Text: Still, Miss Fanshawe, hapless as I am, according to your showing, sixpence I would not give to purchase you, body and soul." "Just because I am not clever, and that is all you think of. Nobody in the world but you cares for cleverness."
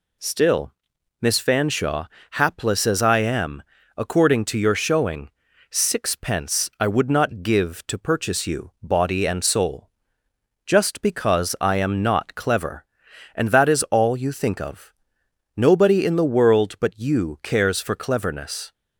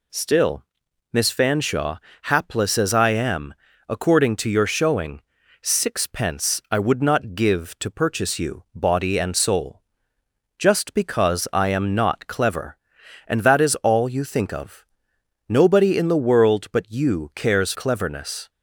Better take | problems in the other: first | skips "for"; at 17.7 s

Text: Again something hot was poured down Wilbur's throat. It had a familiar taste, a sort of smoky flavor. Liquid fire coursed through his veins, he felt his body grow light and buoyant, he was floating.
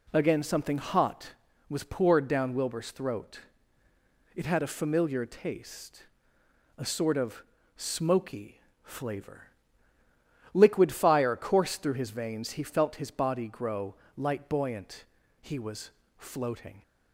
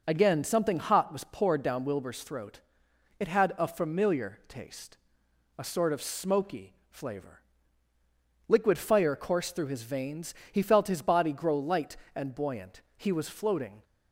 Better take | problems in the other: second | pauses between "of" and "smoky"; slight; at 7.4 s; 0.34 s long // pauses between "smoky" and "flavor"; slight; at 8.6 s; 0.22 s long; slight in the second // pauses between "grow" and "light"; slight; at 13.9 s; 0.22 s long // skips "and"; at 14.4 s // pauses between "was" and "floating"; slight; at 15.9 s; 0.26 s long

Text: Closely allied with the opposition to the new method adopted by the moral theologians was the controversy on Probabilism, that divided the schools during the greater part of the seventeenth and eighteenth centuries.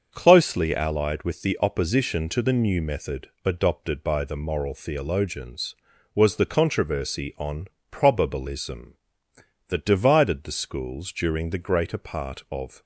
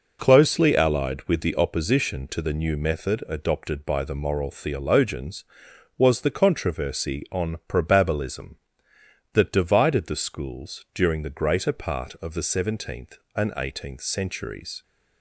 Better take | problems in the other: second | starts louder than the rest; until 1.1 s; 6.5 dB // pauses between "method" and "adopted"; slight; at 3.2 s; 0.16 s long // pauses between "on" and "Probabilism"; slight; at 7.6 s; 0.24 s long // stops before "the seventeenth and eighteenth centuries"; at 12.8 s

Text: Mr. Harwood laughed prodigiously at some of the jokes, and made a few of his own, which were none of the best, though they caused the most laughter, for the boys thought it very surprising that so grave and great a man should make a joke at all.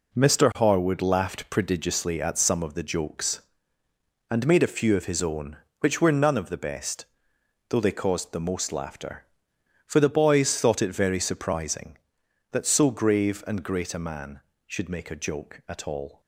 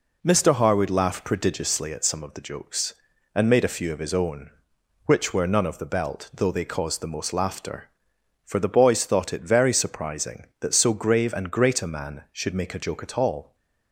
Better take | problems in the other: first | says "belt" for "best"; at 5.8 s

